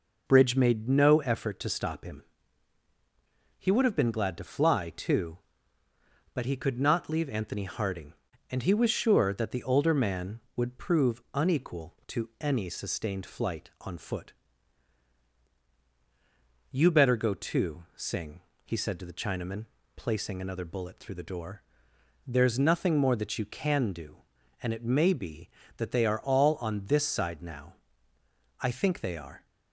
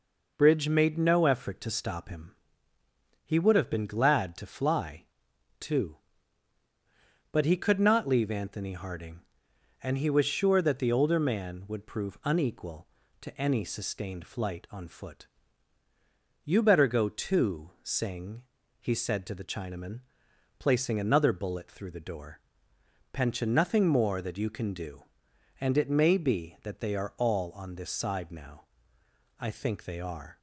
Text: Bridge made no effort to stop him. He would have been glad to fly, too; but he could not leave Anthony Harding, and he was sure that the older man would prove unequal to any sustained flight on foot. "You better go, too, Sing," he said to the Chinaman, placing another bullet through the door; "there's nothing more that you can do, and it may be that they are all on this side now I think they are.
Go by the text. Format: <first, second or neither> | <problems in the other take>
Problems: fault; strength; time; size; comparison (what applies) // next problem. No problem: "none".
first | says "pension" for "there's"; at 23.1 s // pauses between "now" and "I"; noticeable; at 28.6 s; 0.76 s long; noticeable in the first